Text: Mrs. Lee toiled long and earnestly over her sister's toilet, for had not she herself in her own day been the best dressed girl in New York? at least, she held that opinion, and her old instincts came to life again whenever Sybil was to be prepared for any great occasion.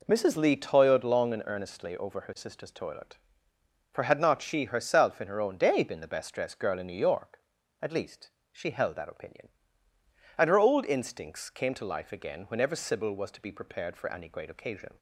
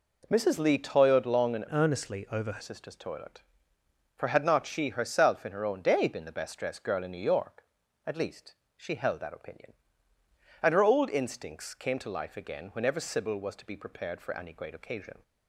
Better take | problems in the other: first | changes voice from "earnestly" to "her"; from 1.7 to 2.6 s; 0.9 s long

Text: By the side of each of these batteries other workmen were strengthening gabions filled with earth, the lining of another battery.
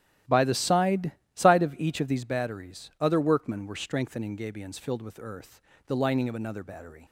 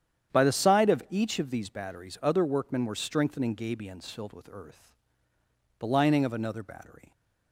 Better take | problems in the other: second | starts louder than the rest; strong; until 1.5 s; 13 dB; strong in the second // says "side" twice; at 1.3 s

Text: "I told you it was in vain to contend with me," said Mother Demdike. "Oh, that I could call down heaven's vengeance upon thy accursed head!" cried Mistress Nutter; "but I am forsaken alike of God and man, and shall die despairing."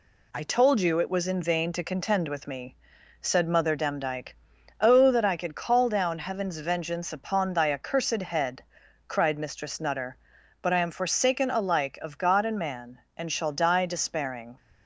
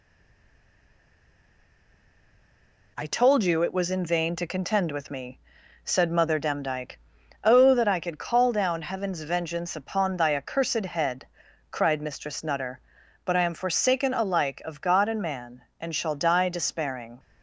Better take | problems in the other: first | stays silent before the first word; strong; until 2.9 s; 2.9 s long

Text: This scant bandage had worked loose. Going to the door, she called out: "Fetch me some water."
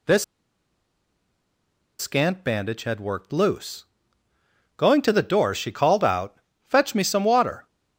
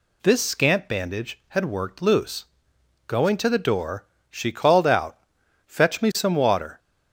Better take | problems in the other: second | pauses between "This" and "scant"; strong; at 0.2 s; 1.7 s long

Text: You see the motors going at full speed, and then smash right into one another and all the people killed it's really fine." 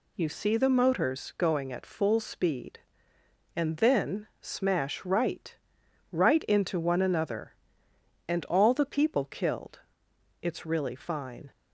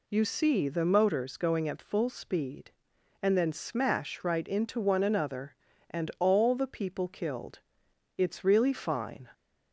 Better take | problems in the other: second | says "right" twice; at 6.1 s // pauses between "killed" and "it's"; noticeable; at 9.7 s; 0.64 s long; noticeable in the second

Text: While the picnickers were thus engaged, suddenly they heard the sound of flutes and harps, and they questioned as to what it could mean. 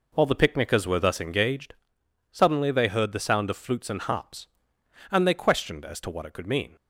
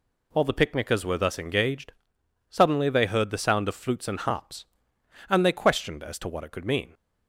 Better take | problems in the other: second | starts louder than the rest; noticeable; until 1.5 s; 4.5 dB

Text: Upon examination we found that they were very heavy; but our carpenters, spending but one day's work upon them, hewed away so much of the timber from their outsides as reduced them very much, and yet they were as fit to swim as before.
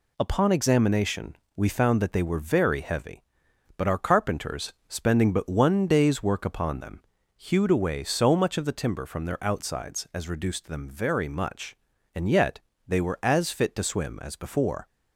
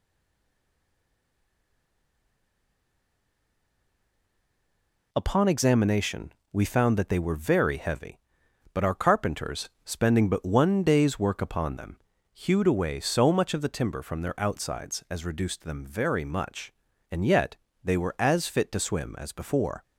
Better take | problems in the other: first | stays silent before the first word; strong; until 5.1 s; 5.1 s long // pauses between "examination" and "we"; slight; at 6.3 s; 0.22 s long; slight in the first // pauses between "yet" and "they"; slight; at 17.5 s; 0.26 s long; slight in the first

